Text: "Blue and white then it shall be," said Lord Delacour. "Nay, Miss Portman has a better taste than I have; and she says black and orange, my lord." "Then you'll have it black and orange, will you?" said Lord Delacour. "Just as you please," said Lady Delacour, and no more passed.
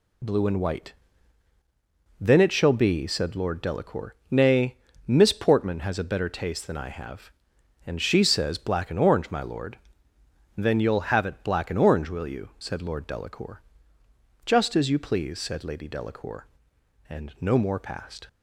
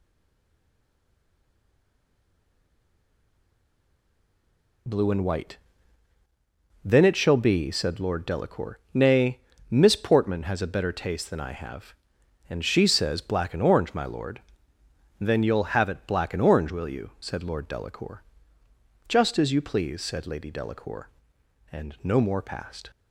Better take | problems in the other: first | stays silent before the first word; strong; until 4.8 s; 4.8 s long // pauses between "white" and "then"; strong; at 5.5 s; 1.2 s long; strong in the first

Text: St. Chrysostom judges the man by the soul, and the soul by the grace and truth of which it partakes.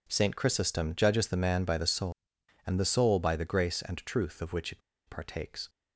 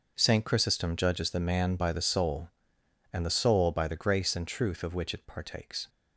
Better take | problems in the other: second | pauses between "it" and "partakes"; slight; at 4.8 s; 0.28 s long

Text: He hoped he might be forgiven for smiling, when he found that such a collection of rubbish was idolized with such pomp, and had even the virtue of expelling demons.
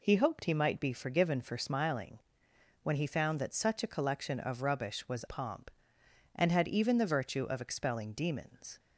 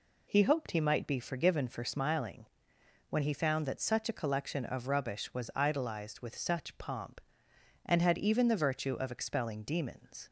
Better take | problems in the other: second | skips "idolized with such"; at 5.2 s

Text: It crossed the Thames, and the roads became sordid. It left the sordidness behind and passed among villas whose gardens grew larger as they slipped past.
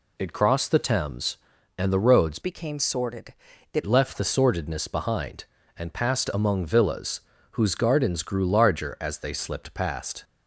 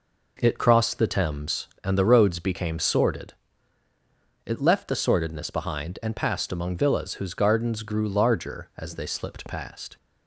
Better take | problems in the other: second | changes voice from "became" to "It"; from 2.4 to 3.8 s; 1.4 s long // pauses between "villas" and "whose"; slight; at 7.2 s; 0.30 s long

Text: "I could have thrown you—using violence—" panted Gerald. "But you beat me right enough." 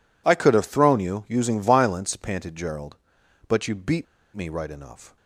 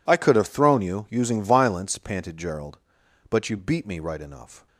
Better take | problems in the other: second | pauses between "beat" and "me"; slight; at 4.0 s; 0.30 s long

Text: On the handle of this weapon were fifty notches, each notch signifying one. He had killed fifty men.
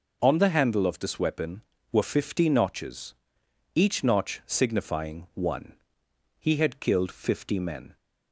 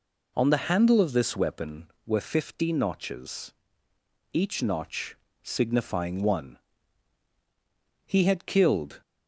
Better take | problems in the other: first | pauses between "notch" and "signifying"; slight; at 5.1 s; 0.26 s long // stops before "fifty men"; at 9.0 s

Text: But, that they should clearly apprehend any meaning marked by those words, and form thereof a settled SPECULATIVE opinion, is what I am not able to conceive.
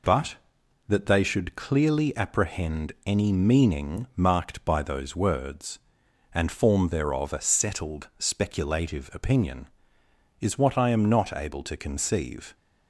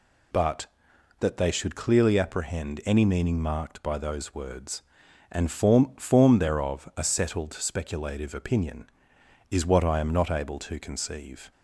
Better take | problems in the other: first | says "form" twice; at 5.9 s

